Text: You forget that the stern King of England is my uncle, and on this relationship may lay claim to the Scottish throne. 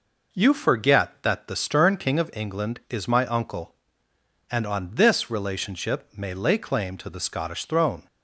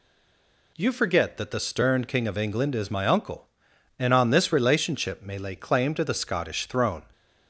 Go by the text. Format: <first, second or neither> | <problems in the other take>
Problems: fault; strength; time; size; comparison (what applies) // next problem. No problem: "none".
first | stays silent before the first word; slight; until 0.7 s; 0.7 s long